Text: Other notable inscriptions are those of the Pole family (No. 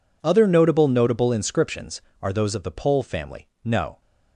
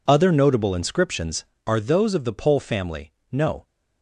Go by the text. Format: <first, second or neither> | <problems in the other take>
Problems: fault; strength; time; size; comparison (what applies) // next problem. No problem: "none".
second | says "notable" twice; at 0.8 s